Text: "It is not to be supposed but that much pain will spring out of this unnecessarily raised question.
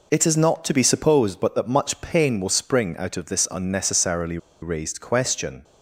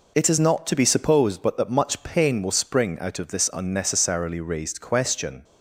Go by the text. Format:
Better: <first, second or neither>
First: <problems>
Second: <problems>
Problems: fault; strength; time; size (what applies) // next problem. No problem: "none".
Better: second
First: pauses between "unnecessarily" and "raised"; slight; at 4.3 s; 0.24 s long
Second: none